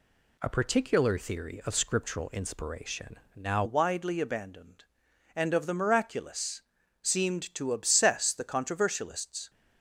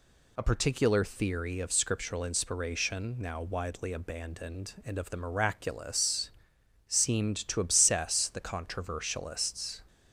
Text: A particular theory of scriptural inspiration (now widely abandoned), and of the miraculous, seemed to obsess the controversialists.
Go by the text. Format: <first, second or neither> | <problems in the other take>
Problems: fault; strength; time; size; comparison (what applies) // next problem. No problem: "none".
second | changes voice at "widely"; from 3.6 s on; 5.8 s long